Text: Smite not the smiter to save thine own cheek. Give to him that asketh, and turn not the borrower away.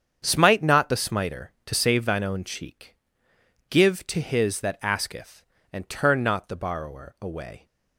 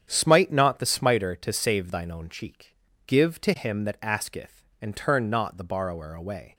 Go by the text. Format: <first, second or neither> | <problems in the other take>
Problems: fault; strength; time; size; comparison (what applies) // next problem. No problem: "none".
second | starts louder than the rest; strong; until 1.2 s; 8 dB; strong in the second // says "his" for "him"; at 4.2 s